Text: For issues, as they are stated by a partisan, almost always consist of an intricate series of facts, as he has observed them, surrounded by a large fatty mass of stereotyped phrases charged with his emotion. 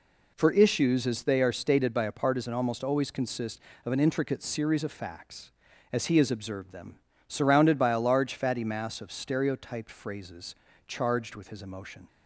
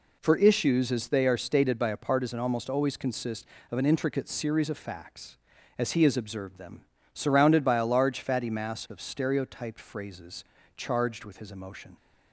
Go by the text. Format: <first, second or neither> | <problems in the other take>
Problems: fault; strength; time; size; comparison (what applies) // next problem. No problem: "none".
neither | pauses between "phrases" and "charged"; slight; the same in both